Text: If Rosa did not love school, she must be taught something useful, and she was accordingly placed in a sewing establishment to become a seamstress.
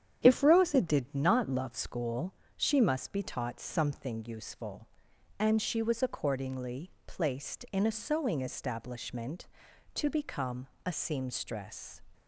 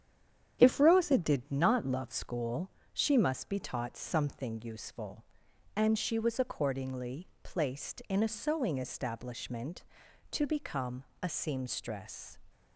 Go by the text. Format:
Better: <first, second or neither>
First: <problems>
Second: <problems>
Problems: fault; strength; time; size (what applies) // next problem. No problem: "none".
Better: first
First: starts louder than the rest; strong; until 1.2 s; 9 dB // pauses between "accordingly" and "placed"; slight; at 6.9 s; 0.16 s long // pauses between "become" and "a"; slight; at 10.6 s; 0.18 s long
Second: stays silent before the first word; slight; until 0.5 s; 0.5 s long // starts louder than the rest; strong; until 1.6 s; 9 dB // pauses between "accordingly" and "placed"; slight; at 7.2 s; 0.16 s long // pauses between "become" and "a"; slight; at 11.0 s; 0.18 s long